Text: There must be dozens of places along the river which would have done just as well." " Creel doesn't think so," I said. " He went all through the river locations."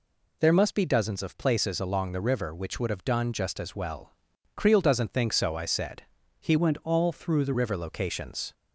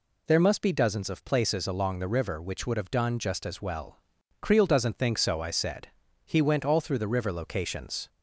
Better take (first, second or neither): second